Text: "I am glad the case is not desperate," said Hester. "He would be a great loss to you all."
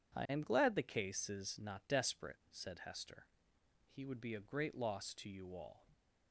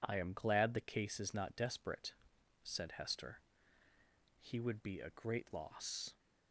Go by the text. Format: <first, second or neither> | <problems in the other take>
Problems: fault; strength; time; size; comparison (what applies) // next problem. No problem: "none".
first | stops before "to you all"; at 6.1 s